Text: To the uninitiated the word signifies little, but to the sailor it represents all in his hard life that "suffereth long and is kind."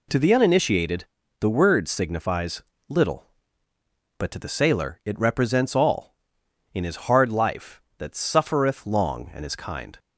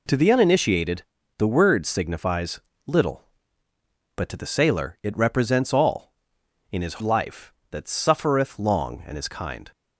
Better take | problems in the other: first | pauses between "uninitiated" and "the"; slight; at 1.0 s; 0.34 s long; slight in the first // pauses between "signifies" and "little"; slight; at 2.6 s; 0.24 s long; slight in the first // skips "hard"; at 7.0 s

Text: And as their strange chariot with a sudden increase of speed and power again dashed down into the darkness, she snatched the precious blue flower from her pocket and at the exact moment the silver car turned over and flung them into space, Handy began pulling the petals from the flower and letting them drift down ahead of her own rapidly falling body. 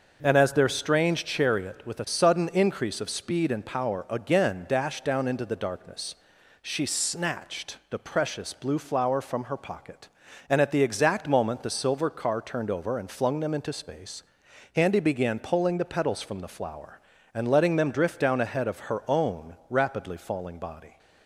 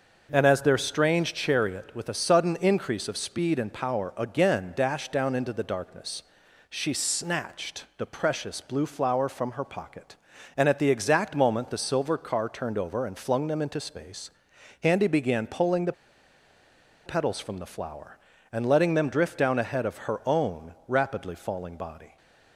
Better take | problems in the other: first | starts louder than the rest; until 1.3 s; 6.5 dB; also in the first // pauses between "the" and "petals"; at 15.9 s; 1.1 s long

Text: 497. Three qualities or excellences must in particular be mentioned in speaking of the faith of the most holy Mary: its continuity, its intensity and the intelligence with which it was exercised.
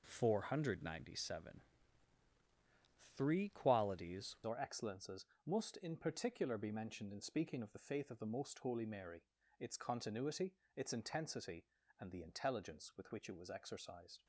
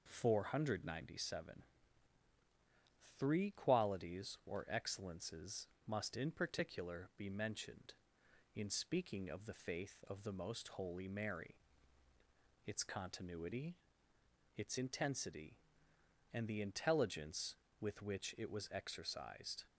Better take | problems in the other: second | changes voice at "or"; from 4.4 s on; 9.8 s long // pauses between "excellences" and "must"; slight; at 5.2 s; 0.20 s long; slight in the second

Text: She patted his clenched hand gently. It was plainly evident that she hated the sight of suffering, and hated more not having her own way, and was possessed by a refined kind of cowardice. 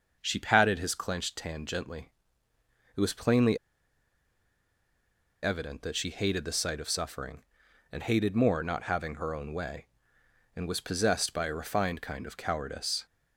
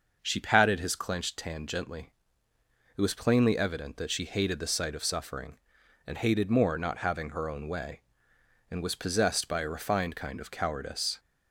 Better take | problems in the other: second | pauses between "plainly" and "evident"; strong; at 3.5 s; 1.8 s long

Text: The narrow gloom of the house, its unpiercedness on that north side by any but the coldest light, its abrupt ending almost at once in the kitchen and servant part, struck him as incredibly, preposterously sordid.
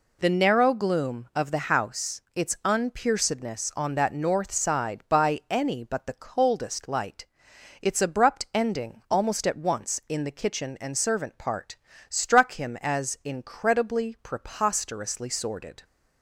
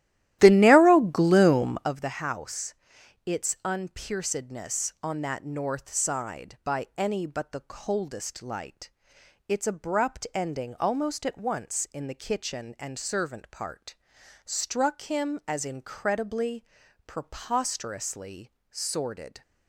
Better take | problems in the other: first | starts louder than the rest; strong; until 1.9 s; 14 dB // pauses between "preposterously" and "sordid"; slight; at 18.4 s; 0.22 s long

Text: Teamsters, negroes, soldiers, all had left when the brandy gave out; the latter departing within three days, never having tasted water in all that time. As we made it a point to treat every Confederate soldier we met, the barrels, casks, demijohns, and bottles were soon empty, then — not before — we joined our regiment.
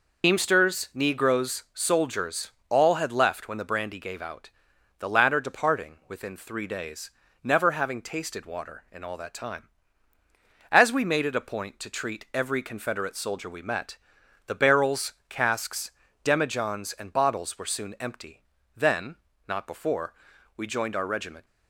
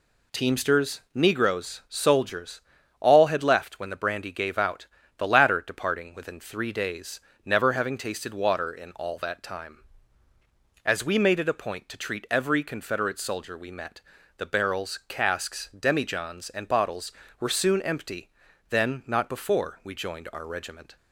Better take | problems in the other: second | loses the start of "Teamsters"; at 0.2 s; 100 ms

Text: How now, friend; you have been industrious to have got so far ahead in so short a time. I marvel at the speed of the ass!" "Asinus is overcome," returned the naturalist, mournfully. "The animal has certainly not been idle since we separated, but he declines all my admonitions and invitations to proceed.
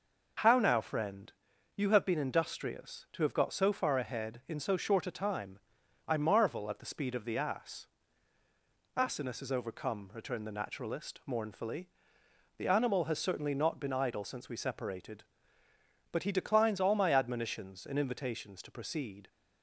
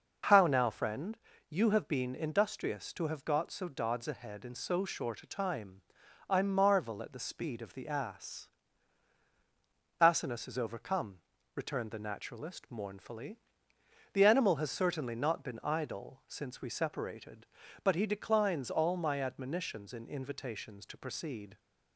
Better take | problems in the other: first | says "dods" for "far"; at 3.6 s

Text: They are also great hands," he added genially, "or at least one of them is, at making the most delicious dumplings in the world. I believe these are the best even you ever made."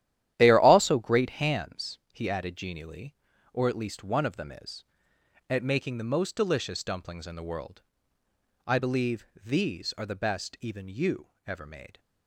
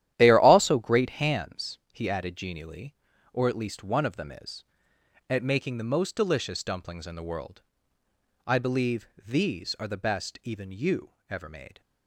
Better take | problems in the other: neither | starts louder than the rest; strong; the same in both // pauses between "believe" and "these"; slight; the same in both // pauses between "you" and "ever"; slight; the same in both

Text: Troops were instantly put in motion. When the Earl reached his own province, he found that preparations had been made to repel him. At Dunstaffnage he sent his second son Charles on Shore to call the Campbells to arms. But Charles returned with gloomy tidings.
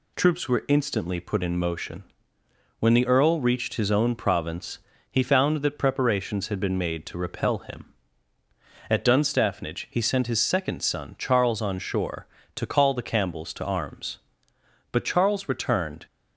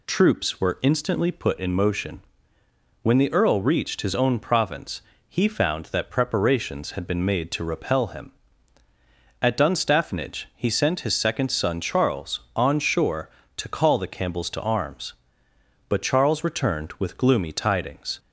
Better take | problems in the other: second | stops before "with gloomy tidings"; at 16.0 s

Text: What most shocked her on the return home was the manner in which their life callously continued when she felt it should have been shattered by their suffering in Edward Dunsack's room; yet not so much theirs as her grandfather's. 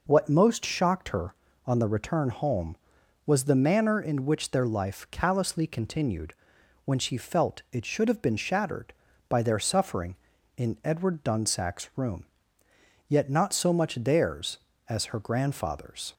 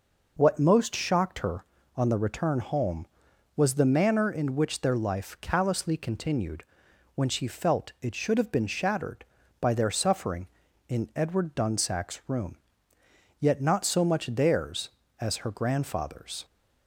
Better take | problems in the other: neither | pauses between "continued" and "when"; noticeable; the same in both

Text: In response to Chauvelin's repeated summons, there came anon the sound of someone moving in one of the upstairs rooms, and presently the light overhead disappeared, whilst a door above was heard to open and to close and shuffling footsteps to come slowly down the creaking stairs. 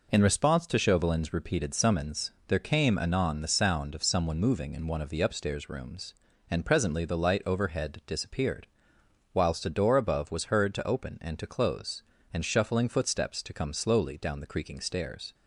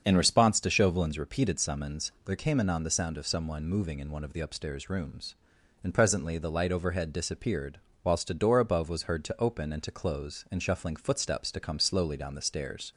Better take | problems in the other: first | starts louder than the rest; until 1.0 s; 7 dB // skips "creaking"; at 12.4 s

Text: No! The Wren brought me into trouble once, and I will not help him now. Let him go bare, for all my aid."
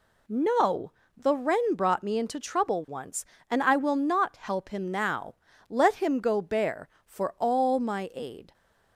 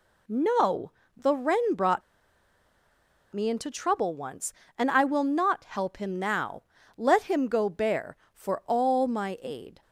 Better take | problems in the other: first | pauses between "brought" and "me"; strong; at 2.0 s; 1.3 s long

